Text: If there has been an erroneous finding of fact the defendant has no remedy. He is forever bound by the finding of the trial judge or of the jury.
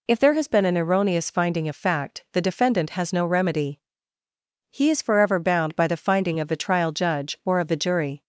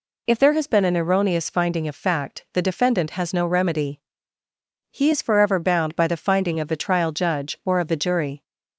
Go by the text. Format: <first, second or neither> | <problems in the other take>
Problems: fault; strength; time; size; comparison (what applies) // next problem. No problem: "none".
neither | none